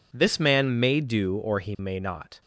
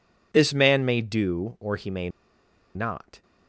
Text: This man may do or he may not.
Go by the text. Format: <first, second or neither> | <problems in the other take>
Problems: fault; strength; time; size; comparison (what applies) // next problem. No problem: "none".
first | pauses between "may" and "not"; noticeable; at 2.0 s; 0.65 s long